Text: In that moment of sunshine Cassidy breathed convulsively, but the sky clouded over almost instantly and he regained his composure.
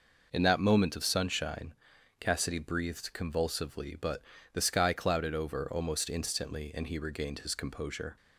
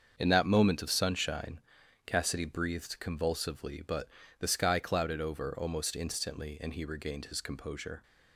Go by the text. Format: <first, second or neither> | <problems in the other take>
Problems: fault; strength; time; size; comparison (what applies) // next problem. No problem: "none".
first | gets quieter; strong; throughout; 8 dB // pauses between "sunshine" and "Cassidy"; at 1.6 s; 0.44 s long; also in the first // pauses between "but" and "the"; slight; at 4.0 s; 0.32 s long; slight in the first